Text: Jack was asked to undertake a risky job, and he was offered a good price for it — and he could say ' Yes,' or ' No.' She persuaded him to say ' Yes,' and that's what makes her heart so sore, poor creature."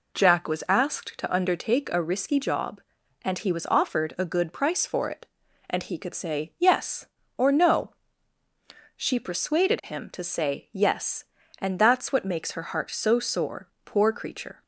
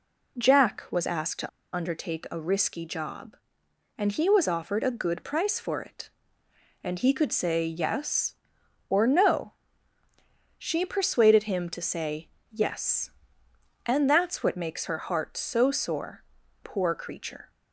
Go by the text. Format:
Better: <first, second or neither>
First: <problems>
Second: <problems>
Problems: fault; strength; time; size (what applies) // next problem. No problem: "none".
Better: first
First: none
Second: pauses between "to" and "undertake"; slight; at 1.4 s; 0.26 s long